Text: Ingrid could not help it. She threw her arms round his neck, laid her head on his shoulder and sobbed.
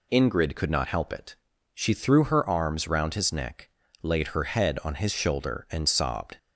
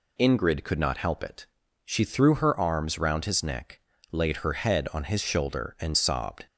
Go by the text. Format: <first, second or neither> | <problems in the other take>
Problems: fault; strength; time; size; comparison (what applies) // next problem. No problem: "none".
neither | none